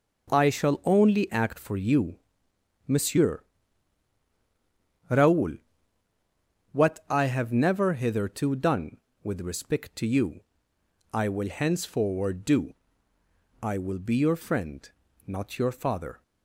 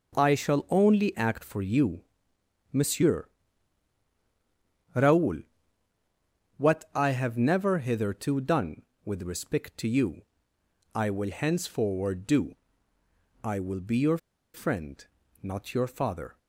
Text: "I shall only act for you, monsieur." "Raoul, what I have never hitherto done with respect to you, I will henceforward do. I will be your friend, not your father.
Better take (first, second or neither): first